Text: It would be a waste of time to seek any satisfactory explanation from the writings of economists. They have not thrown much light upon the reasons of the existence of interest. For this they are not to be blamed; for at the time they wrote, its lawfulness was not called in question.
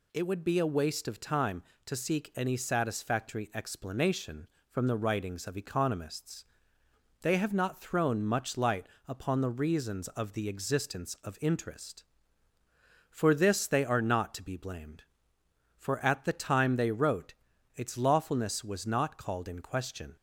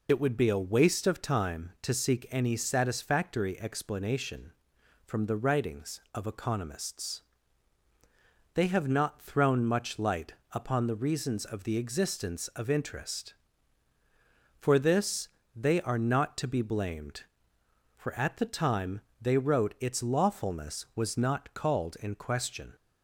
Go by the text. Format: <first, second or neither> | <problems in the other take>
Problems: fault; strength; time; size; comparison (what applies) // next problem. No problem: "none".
first | loses the start of "It"; at 0.0 s; 40 ms // pauses between "light" and "upon"; slight; at 10.3 s; 0.18 s long; slight in the first // pauses between "this" and "they"; slight; at 15.2 s; 0.26 s long // pauses between "time" and "they"; slight; at 18.9 s; 0.22 s long